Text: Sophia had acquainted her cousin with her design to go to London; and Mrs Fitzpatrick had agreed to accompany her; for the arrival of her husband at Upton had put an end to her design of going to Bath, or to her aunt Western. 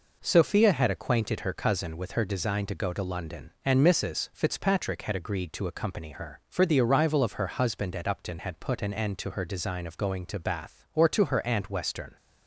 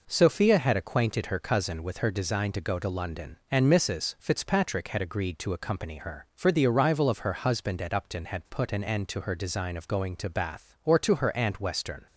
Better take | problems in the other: neither | none

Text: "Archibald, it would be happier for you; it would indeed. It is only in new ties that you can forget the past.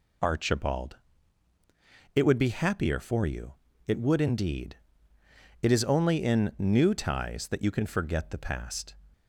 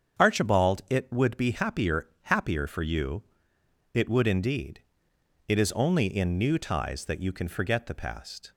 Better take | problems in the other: first | starts louder than the rest; strong; until 1.2 s; 7.5 dB // says "happier" twice; at 2.2 s

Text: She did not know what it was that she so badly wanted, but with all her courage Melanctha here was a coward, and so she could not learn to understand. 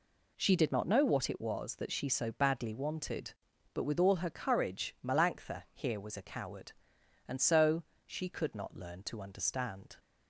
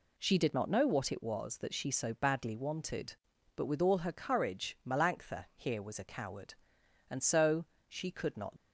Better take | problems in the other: first | pauses between "so" and "she"; slight; at 7.6 s; 0.22 s long; slight in the first // stops before "learn to understand"; at 8.5 s

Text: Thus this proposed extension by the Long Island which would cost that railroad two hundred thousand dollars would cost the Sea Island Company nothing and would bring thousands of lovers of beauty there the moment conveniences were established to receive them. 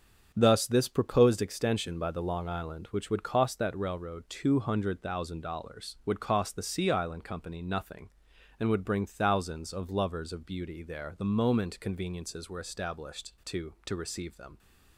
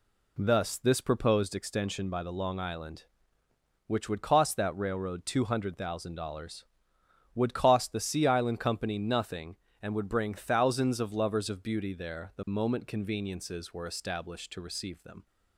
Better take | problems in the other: second | starts louder than the rest; strong; until 1.3 s; 7 dB // says "to" twice; at 13.8 s

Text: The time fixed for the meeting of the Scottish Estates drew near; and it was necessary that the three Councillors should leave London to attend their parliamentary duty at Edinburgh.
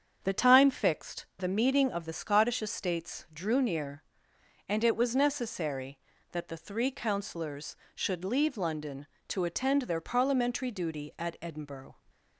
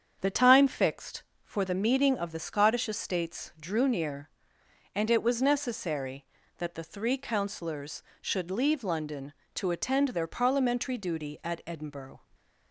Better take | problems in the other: second | starts louder than the rest; strong; until 1.2 s; 7.5 dB; strong in the second // skips "for"; at 1.3 s

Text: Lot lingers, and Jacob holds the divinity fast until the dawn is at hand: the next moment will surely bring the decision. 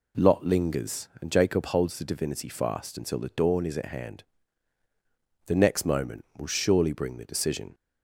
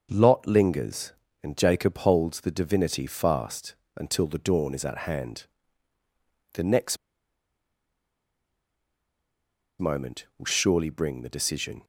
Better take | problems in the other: first | starts louder than the rest; until 1.1 s; 6 dB // pauses between "fast" and "until"; slight; at 3.7 s; 0.20 s long // pauses between "next" and "moment"; strong; at 6.9 s; 2.8 s long

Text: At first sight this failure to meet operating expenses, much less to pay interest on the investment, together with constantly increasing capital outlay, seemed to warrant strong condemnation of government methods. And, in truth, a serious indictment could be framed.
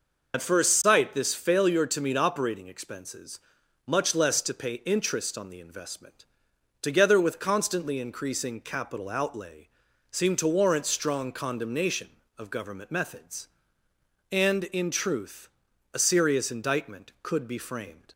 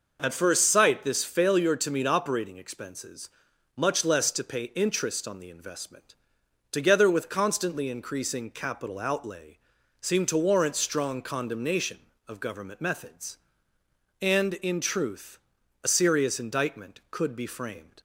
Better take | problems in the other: second | loses the start of "At"; at 0.3 s; 60 ms

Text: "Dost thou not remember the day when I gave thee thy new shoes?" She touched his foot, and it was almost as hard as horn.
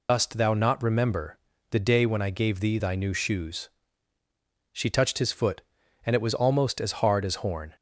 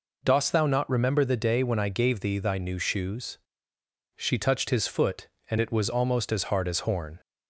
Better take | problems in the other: second | loses the start of "Dost"; at 0.0 s; 95 ms // pauses between "remember" and "the"; slight; at 1.3 s; 0.32 s long

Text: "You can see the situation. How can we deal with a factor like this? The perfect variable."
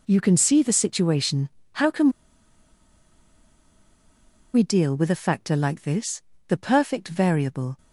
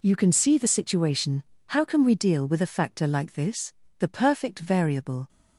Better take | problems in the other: second | pauses between "can" and "we"; strong; at 2.0 s; 2.4 s long

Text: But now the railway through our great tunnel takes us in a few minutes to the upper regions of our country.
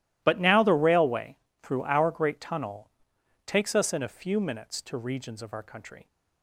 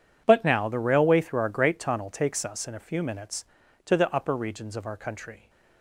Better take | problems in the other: second | pauses between "railway" and "through"; slight; at 1.3 s; 0.26 s long // pauses between "tunnel" and "takes"; noticeable; at 2.9 s; 0.56 s long // skips "the upper"; at 4.9 s

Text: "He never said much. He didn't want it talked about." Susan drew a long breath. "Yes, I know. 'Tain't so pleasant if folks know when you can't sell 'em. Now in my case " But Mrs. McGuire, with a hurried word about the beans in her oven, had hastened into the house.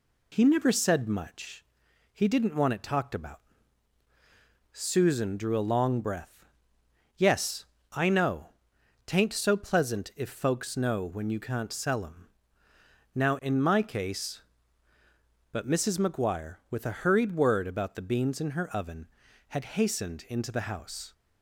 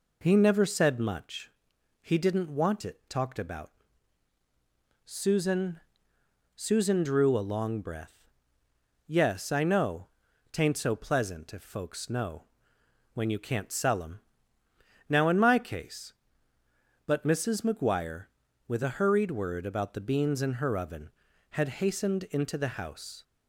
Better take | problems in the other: first | says "Susan" twice; at 6.5 s // pauses between "know" and "when"; noticeable; at 12.4 s; 0.70 s long

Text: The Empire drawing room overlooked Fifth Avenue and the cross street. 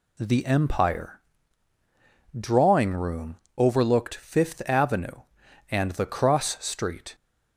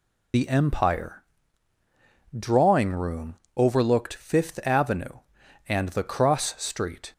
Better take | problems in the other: first | loses the start of "The"; at 0.3 s; 120 ms // pauses between "Empire" and "drawing"; at 1.2 s; 1.1 s long; also in the first // pauses between "room" and "overlooked"; slight; at 3.3 s; 0.20 s long; slight in the first

